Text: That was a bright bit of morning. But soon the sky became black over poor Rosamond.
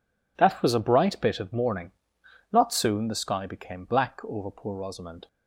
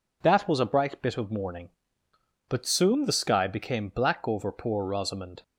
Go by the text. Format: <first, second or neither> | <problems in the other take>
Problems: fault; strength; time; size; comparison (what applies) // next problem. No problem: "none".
second | says "Not" for "But"; at 2.5 s